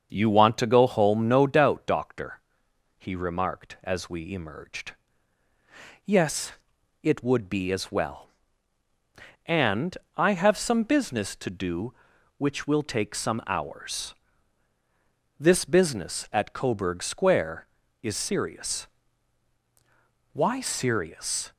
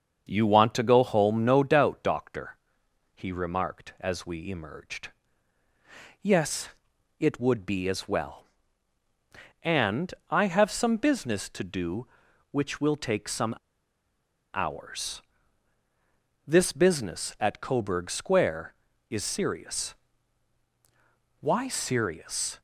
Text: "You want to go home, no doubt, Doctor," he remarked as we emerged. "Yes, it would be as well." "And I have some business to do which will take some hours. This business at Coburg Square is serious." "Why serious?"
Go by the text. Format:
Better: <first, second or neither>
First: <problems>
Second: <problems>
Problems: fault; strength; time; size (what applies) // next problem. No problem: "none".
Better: first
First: starts louder than the rest; until 1.1 s; 6.5 dB // pauses between "And" and "I"; slight; at 9.9 s; 0.19 s long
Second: starts louder than the rest; until 1.3 s; 6.5 dB // pauses between "And" and "I"; slight; at 10.1 s; 0.16 s long // pauses between "some" and "hours"; at 13.5 s; 1.0 s long